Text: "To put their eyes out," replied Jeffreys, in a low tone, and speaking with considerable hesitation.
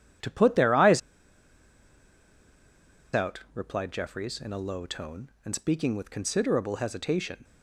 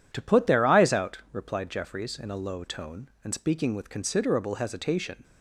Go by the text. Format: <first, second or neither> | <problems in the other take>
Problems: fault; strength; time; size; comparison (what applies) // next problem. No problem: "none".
second | pauses between "eyes" and "out"; strong; at 1.0 s; 2.1 s long